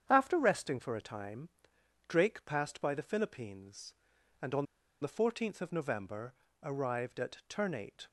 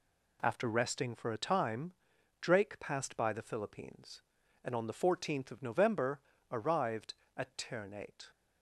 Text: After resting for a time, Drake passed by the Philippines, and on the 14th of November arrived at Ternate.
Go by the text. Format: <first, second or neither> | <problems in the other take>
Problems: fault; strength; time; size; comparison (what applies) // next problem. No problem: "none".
second | starts louder than the rest; strong; until 1.0 s; 8.5 dB // pauses between "on" and "the"; at 4.6 s; 0.37 s long // pauses between "November" and "arrived"; slight; at 6.3 s; 0.30 s long; slight in the second